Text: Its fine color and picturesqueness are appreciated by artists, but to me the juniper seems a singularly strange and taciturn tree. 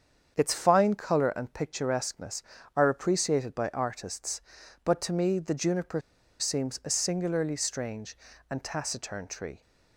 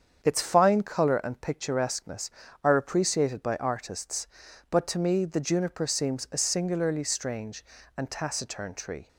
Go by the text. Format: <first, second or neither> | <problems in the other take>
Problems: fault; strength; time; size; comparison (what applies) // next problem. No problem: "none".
second | starts louder than the rest; strong; until 1.3 s; 7.5 dB; strong in the second // pauses between "juniper" and "seems"; at 6.0 s; 0.39 s long